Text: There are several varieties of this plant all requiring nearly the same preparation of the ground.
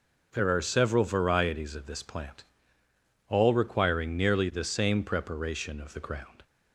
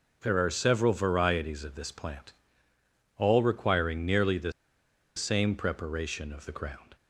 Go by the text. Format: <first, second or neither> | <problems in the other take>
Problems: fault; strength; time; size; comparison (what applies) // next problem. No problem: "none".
first | pauses between "plant" and "all"; noticeable; at 2.3 s; 0.82 s long; noticeable in the first // pauses between "the" and "same"; noticeable; at 4.5 s; 0.64 s long